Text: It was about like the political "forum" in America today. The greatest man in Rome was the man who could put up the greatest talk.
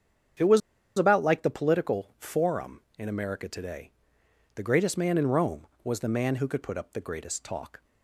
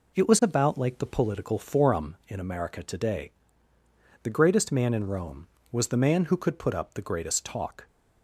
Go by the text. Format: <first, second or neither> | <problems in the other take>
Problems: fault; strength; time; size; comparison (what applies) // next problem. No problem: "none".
second | starts louder than the rest; strong; until 1.7 s; 7.5 dB // pauses between "was" and "about"; at 0.6 s; 0.37 s long